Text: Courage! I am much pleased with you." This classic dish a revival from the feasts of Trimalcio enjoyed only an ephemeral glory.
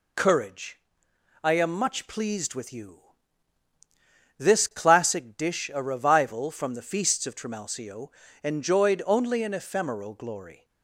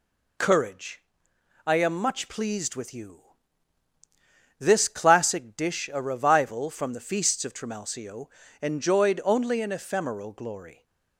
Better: neither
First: pauses between "Trimalcio" and "enjoyed"; slight; at 8.0 s; 0.34 s long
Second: pauses between "Trimalcio" and "enjoyed"; slight; at 8.2 s; 0.34 s long

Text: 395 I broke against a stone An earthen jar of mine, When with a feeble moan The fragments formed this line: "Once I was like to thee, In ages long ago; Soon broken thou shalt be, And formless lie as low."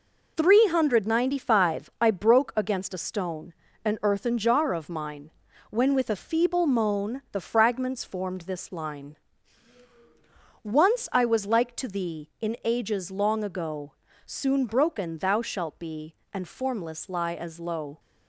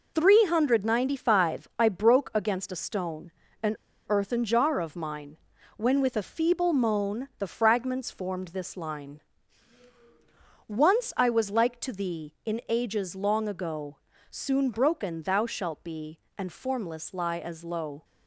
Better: first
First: pauses between "stone" and "An"; slight; at 3.5 s; 0.32 s long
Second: pauses between "stone" and "An"; slight; at 3.2 s; 0.32 s long // pauses between "An" and "earthen"; slight; at 3.7 s; 0.32 s long

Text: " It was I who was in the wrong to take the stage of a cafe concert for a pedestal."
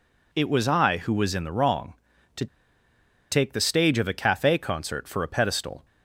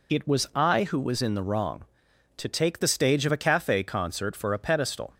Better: second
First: pauses between "to" and "take"; noticeable; at 2.4 s; 0.85 s long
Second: none

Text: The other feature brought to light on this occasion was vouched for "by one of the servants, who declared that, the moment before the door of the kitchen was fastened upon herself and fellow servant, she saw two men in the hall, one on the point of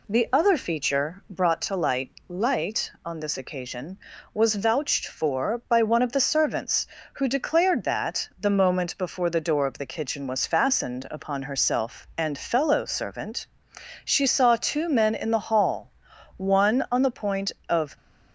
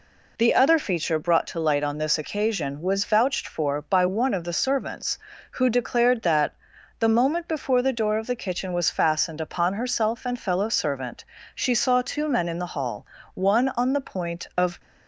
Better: second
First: says "light" twice; at 2.2 s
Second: none

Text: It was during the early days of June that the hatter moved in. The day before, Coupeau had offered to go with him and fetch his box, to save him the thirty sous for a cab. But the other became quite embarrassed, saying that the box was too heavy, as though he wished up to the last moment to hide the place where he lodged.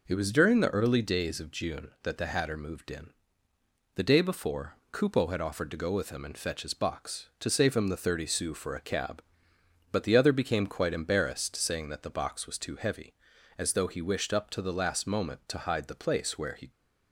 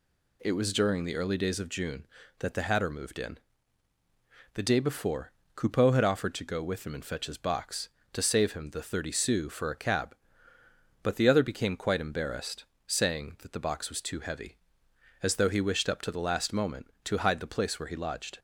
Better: second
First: stops before "lodged"; at 16.7 s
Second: none

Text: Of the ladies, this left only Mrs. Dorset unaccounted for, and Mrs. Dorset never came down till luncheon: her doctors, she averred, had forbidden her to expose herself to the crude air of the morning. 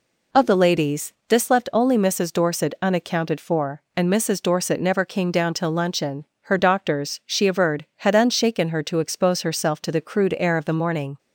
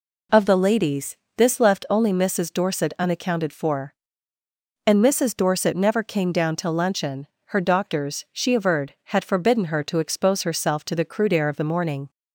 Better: second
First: says "unshaken" for "forbidden"; at 8.1 s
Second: none

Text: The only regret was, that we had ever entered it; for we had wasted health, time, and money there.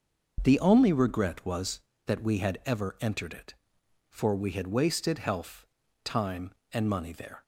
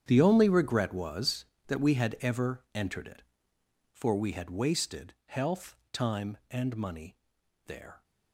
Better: first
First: starts louder than the rest; until 1.4 s; 6 dB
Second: gets quieter; strong; throughout; 17 dB // starts louder than the rest; strong; until 1.0 s; 9 dB // pauses between "money" and "there"; noticeable; at 7.1 s; 0.48 s long

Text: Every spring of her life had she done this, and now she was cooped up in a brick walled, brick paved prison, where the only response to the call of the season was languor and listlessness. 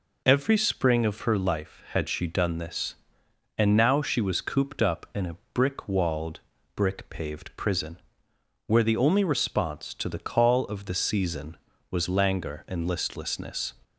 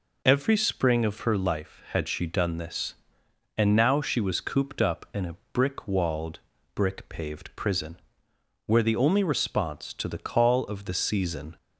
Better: first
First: pauses between "a" and "brick"; slight; at 5.3 s; 0.18 s long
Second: pauses between "a" and "brick"; slight; at 5.3 s; 0.18 s long // stops before "was languor and listlessness"; at 11.5 s

